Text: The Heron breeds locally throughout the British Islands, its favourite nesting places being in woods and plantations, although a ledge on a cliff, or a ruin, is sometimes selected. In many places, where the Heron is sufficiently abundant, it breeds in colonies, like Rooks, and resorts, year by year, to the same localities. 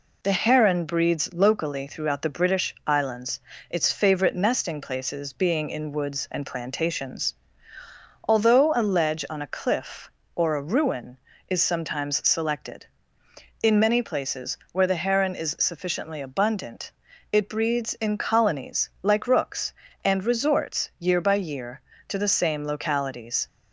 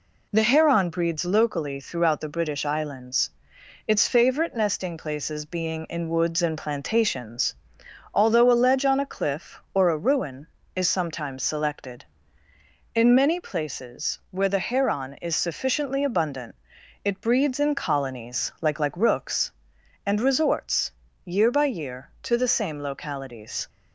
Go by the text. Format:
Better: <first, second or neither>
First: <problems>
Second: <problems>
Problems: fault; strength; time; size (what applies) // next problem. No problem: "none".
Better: first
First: none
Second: says "like" twice; at 18.8 s